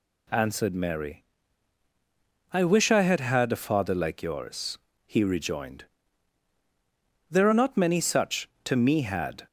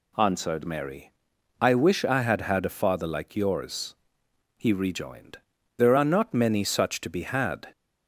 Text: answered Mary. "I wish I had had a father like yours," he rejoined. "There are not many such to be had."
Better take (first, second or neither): second